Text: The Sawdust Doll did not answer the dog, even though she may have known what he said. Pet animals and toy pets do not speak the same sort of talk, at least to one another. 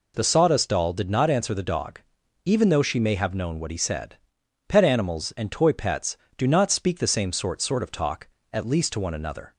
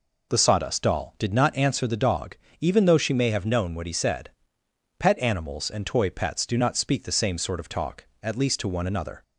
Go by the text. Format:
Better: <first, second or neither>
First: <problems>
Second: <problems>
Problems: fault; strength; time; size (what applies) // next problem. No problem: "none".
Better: second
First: says "sort" twice; at 7.6 s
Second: none